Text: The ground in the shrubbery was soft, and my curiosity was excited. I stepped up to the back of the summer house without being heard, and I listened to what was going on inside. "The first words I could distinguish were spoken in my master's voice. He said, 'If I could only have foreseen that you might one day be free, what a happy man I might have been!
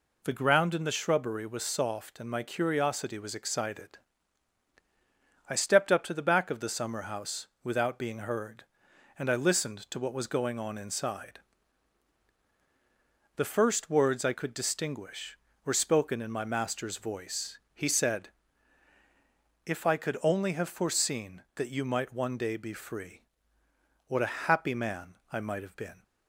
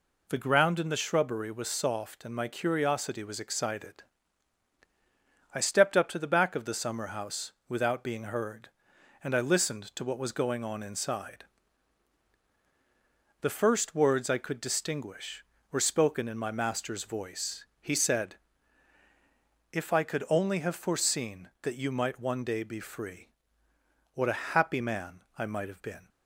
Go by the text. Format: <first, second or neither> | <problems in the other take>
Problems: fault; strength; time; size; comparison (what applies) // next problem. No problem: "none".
neither | pauses between "house" and "without"; slight; the same in both // pauses between "man" and "I"; slight; the same in both